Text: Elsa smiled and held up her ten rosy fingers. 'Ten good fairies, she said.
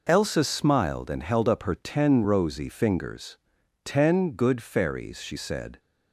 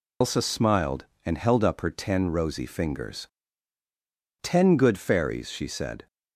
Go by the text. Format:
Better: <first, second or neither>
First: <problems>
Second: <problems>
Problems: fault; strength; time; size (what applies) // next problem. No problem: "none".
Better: first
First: none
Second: loses the start of "Elsa"; at 0.2 s; 110 ms